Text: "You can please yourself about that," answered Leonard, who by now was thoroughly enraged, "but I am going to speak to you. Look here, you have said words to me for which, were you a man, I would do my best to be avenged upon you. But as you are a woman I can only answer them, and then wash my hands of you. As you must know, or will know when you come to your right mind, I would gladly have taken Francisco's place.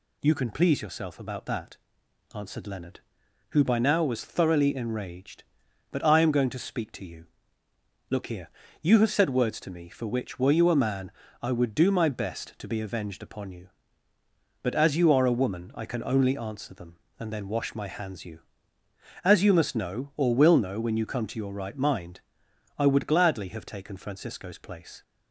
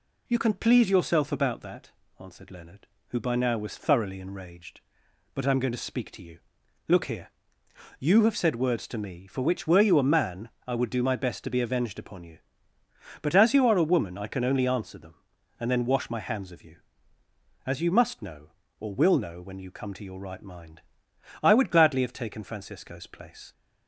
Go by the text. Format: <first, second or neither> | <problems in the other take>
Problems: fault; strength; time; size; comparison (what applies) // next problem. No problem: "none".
second | skips "of"; at 18.2 s